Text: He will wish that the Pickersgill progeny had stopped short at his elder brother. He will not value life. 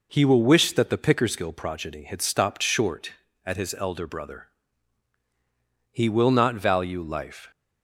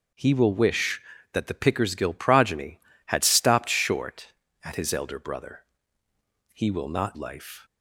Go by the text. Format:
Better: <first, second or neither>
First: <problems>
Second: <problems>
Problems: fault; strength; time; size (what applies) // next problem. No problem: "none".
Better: first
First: none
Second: skips "value"; at 7.1 s